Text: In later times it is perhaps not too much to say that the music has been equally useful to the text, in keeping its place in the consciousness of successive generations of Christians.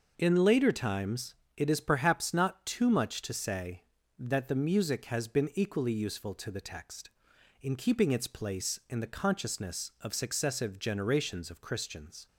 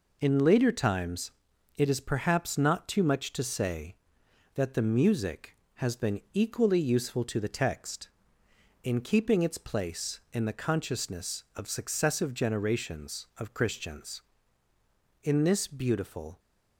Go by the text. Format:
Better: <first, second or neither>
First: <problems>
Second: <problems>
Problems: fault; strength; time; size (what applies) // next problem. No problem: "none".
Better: first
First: pauses between "times" and "it"; slight; at 1.3 s; 0.24 s long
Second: pauses between "times" and "it"; noticeable; at 1.3 s; 0.46 s long // goes on to say "In this beautiful"; noticeable; from 15.2 s on; 1.1 s long